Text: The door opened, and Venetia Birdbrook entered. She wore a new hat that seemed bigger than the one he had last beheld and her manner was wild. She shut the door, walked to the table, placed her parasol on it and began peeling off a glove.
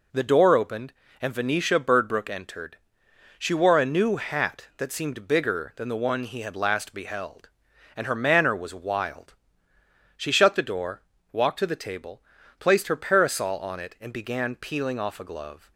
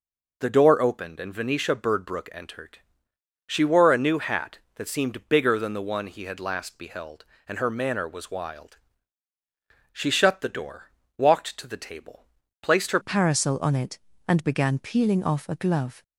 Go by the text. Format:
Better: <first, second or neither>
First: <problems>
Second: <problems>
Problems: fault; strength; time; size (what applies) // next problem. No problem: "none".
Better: first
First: none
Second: changes voice at "parasol"; from 13.0 s on; 3.0 s long